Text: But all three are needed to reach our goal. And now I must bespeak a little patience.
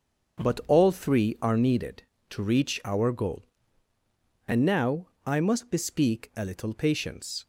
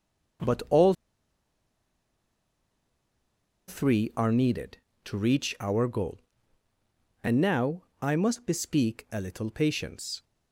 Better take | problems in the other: first | starts louder than the rest; until 4.3 s; 7 dB; also in the first // pauses between "all" and "three"; strong; at 0.9 s; 2.7 s long // pauses between "now" and "I"; slight; at 7.8 s; 0.18 s long; slight in the first

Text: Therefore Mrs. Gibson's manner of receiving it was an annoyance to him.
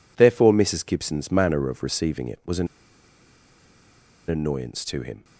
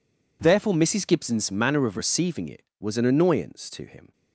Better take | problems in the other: second | pauses between "an" and "annoyance"; strong; at 2.6 s; 1.6 s long

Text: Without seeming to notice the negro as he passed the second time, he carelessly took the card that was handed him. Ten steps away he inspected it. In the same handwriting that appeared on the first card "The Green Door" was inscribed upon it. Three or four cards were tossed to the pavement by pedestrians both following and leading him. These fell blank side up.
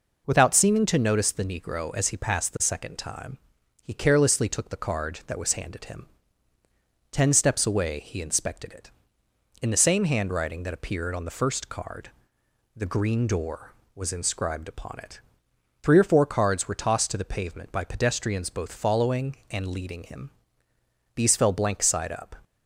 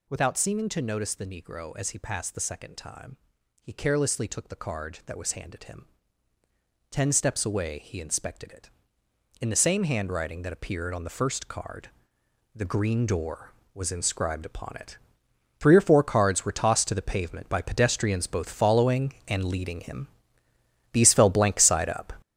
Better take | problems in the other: first | gets louder; strong; throughout; 8 dB // pauses between "card" and "The"; noticeable; at 11.8 s; 0.66 s long; noticeable in the first

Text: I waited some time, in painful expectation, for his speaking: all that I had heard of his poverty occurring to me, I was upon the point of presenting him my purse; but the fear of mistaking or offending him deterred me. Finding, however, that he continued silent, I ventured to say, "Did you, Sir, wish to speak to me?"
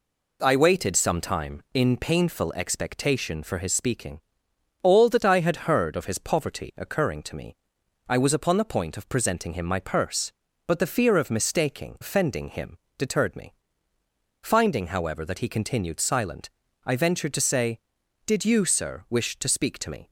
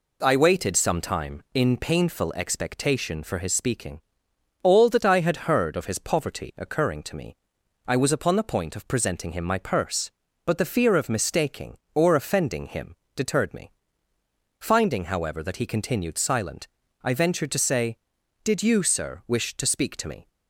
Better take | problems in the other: second | skips "or"; at 11.9 s // pauses between "him" and "deterred"; slight; at 12.7 s; 0.20 s long; slight in the second

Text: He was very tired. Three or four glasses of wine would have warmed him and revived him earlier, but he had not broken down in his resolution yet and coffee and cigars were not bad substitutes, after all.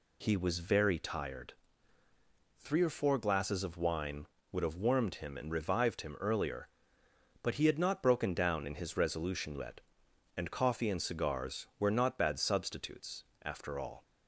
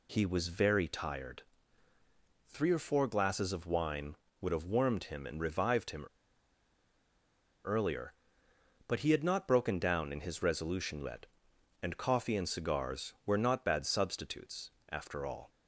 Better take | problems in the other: first | pauses between "him" and "earlier"; strong; at 6.0 s; 1.6 s long

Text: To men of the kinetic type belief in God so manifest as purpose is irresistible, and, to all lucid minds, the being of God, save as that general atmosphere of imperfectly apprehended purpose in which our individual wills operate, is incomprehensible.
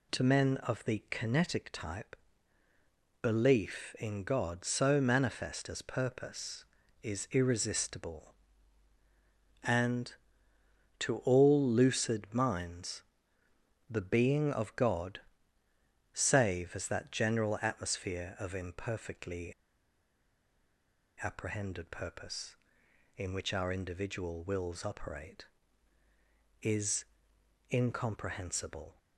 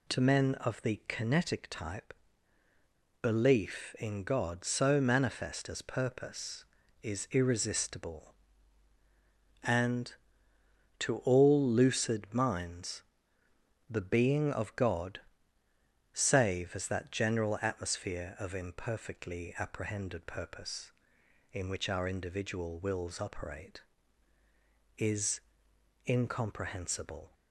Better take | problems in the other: second | pauses between "type" and "belief"; at 2.1 s; 1.0 s long; also in the second // pauses between "imperfectly" and "apprehended"; strong; at 19.5 s; 1.7 s long // pauses between "is" and "incomprehensible"; noticeable; at 27.0 s; 0.66 s long; noticeable in the second

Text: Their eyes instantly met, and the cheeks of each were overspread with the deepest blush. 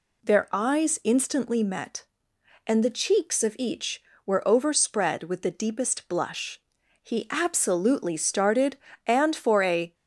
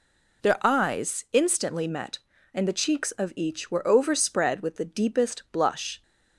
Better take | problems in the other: second | goes on to say "He absolutely started and for a"; strong; from 7.0 s on; 2.9 s long

